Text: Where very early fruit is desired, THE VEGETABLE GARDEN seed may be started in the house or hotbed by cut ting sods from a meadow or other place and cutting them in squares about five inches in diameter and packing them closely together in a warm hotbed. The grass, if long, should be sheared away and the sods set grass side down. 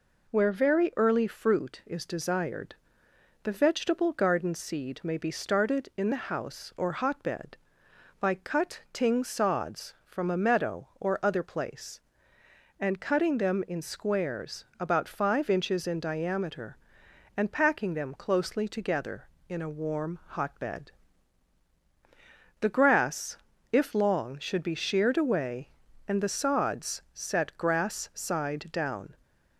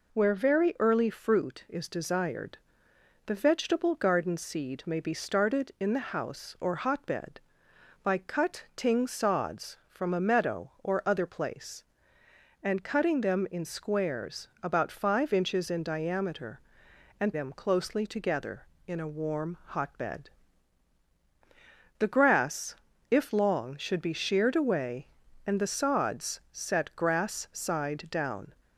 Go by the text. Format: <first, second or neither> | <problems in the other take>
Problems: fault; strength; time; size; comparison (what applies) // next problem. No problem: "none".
first | pauses between "squares" and "about"; slight; at 14.4 s; 0.16 s long; slight in the first // skips "packing"; at 17.3 s